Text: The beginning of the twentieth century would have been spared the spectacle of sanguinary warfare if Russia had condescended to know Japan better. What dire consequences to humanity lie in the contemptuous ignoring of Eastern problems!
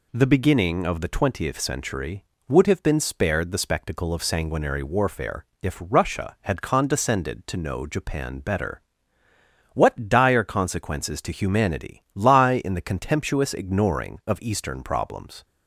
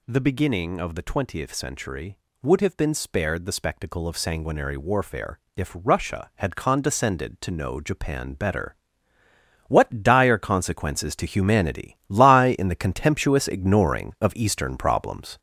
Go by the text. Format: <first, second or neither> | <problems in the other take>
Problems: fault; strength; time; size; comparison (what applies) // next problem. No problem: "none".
first | gets louder; throughout; 6.5 dB // pauses between "warfare" and "if"; slight; at 5.3 s; 0.16 s long; slight in the first